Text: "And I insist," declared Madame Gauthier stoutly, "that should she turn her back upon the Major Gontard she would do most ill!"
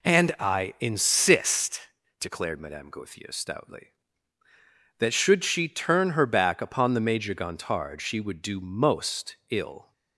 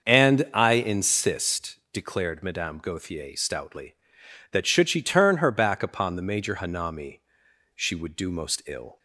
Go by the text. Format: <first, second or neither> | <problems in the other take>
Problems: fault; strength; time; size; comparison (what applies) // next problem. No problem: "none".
first | starts louder than the rest; until 1.0 s; 6.5 dB // says "Hanami" for "Gontard"; at 6.5 s